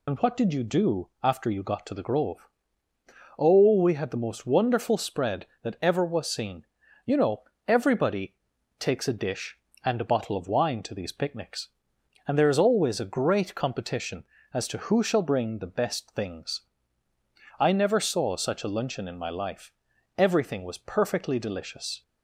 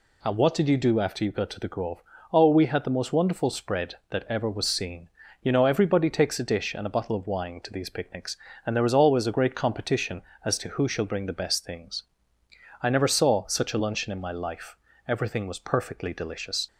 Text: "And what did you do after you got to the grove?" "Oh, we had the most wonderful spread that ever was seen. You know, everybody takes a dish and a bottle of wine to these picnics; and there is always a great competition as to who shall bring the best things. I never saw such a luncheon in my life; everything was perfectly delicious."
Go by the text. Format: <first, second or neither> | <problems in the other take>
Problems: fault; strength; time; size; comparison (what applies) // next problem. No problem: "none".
second | loses the start of "And"; at 0.0 s; 50 ms // pauses between "everybody" and "takes"; at 8.3 s; 0.42 s long